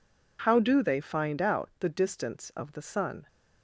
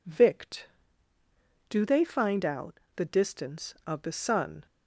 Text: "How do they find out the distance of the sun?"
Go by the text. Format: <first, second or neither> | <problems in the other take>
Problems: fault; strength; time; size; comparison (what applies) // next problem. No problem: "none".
first | says "Vict" for "How"; at 0.0 s // pauses between "out" and "the"; slight; at 2.7 s; 0.16 s long